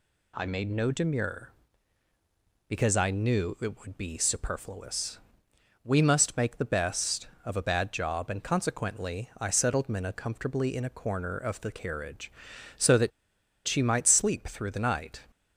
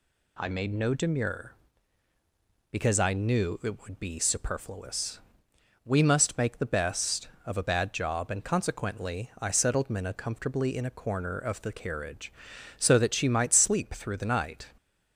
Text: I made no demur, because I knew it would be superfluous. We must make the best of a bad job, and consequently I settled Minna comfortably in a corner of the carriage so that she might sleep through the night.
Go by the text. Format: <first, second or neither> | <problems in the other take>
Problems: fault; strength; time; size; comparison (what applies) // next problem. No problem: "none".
second | pauses between "that" and "she"; noticeable; at 13.1 s; 0.56 s long